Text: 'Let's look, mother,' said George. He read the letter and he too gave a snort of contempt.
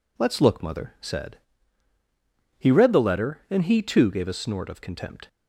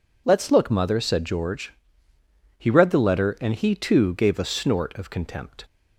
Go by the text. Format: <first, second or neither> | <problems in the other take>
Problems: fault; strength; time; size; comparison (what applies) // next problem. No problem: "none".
second | skips "George"; at 1.9 s